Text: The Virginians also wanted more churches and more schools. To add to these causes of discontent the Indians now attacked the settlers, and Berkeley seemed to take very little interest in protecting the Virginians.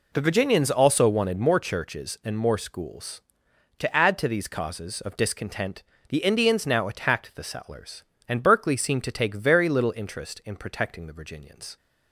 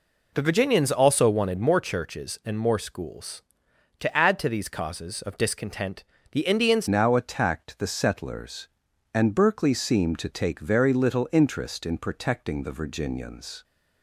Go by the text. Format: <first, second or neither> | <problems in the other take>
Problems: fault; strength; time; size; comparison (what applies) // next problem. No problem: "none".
first | pauses between "discontent" and "the"; slight; at 6.0 s; 0.28 s long; slight in the first // changes voice at "now"; from 6.8 s on; 6.8 s long